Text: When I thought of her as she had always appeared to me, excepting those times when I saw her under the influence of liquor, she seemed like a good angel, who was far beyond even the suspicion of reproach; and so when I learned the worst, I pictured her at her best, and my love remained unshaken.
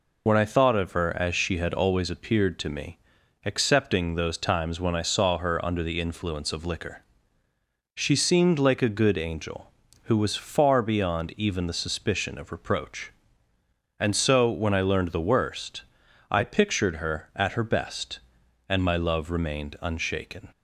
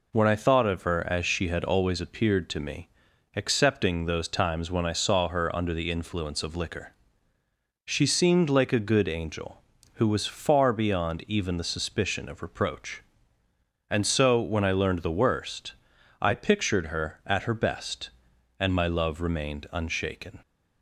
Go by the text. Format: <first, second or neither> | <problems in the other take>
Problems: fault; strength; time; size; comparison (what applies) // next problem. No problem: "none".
second | loses the start of "When"; at 0.2 s; 40 ms